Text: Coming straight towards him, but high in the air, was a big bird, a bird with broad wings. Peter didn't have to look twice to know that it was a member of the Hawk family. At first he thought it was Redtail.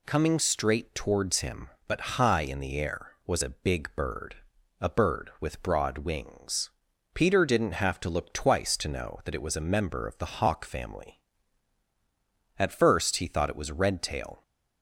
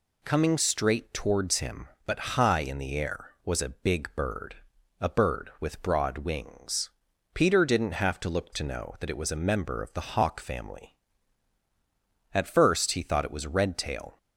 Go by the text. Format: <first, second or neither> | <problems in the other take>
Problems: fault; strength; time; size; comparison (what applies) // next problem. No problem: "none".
first | skips "twice"; at 8.5 s